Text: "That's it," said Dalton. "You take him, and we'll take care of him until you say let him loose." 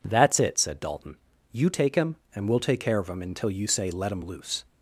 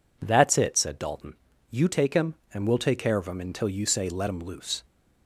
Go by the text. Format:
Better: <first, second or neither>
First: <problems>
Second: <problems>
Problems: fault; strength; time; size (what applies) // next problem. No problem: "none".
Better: neither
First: none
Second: none